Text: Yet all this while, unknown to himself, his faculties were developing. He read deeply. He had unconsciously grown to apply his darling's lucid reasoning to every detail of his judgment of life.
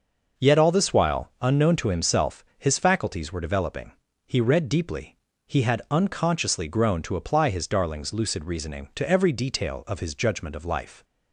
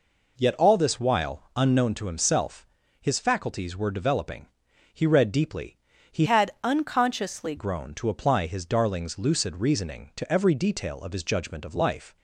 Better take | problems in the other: first | changes voice from "had" to "unconsciously"; from 6.2 to 7.5 s; 1.3 s long

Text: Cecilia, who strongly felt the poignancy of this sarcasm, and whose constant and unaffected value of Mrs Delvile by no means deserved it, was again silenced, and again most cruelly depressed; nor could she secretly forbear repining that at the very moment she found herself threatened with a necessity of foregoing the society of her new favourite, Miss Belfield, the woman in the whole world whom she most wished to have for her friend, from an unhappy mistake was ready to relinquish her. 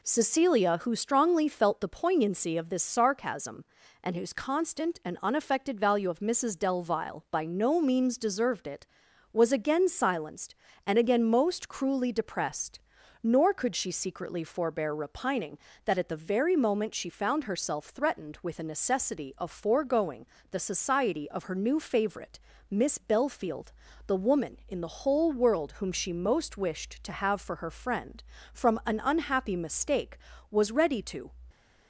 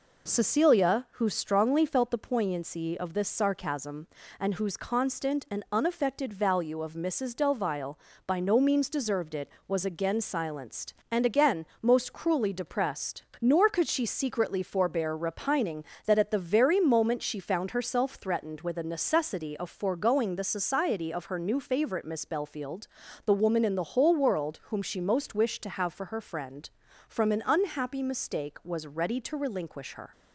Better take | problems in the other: second | pauses between "foregoing" and "the"; slight; at 20.2 s; 0.26 s long // stops before "relinquish her"; at 31.5 s

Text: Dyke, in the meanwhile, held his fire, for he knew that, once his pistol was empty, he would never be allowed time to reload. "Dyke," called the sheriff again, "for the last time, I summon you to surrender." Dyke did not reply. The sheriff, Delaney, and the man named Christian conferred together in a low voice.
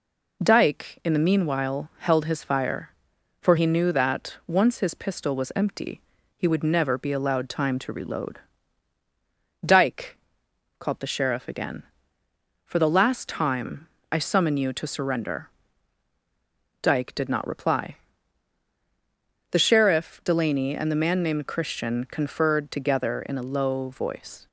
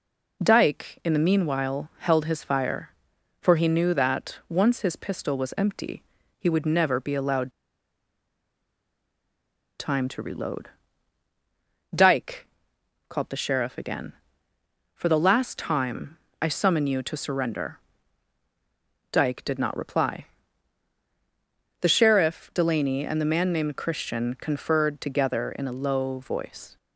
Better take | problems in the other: first | pauses between "allowed" and "time"; strong; at 7.5 s; 2.2 s long

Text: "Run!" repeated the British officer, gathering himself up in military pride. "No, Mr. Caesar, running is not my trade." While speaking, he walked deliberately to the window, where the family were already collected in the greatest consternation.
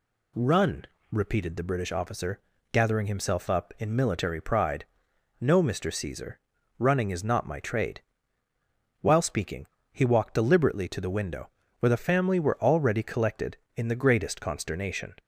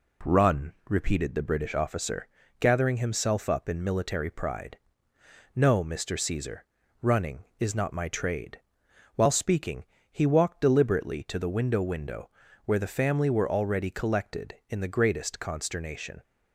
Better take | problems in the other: first | says "window" twice; at 11.8 s

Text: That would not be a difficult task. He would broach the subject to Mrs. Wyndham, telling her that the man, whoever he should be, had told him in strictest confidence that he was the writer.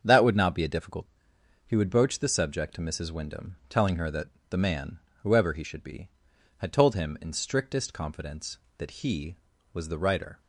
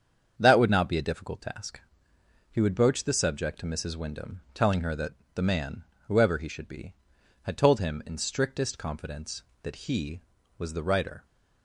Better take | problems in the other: second | starts louder than the rest; until 1.0 s; 7 dB; strong in the second // skips "task"; at 1.3 s // pauses between "that" and "the"; slight; at 4.2 s; 0.22 s long; slight in the second

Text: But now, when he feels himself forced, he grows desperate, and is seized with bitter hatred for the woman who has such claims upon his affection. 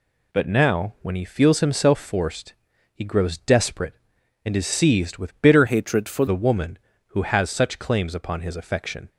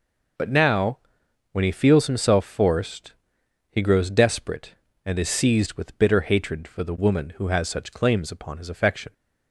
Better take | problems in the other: second | changes voice from "hatred" to "for"; from 5.6 to 6.2 s; 0.6 s long

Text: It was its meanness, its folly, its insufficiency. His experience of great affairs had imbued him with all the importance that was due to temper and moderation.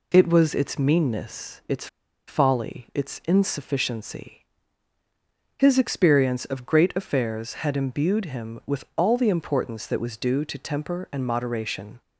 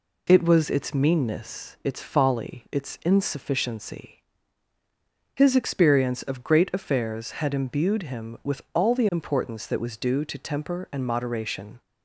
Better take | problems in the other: second | pauses between "its" and "folly"; at 1.8 s; 0.40 s long

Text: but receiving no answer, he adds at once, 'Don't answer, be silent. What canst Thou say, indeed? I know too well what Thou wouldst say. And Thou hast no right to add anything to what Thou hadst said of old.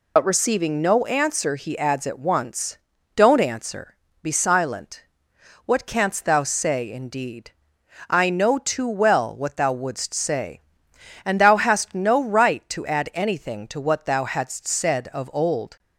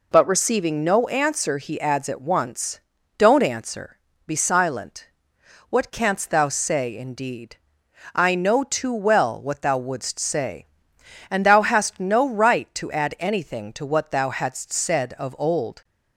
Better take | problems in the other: second | loses the start of "but"; at 0.1 s; 55 ms

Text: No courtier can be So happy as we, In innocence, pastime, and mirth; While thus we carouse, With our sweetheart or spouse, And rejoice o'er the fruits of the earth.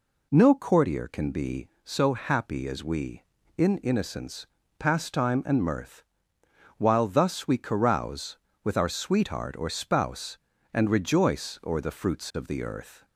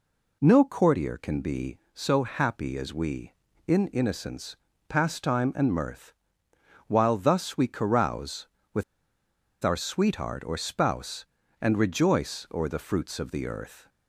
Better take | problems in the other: first | pauses between "With" and "our"; noticeable; at 8.8 s; 0.80 s long

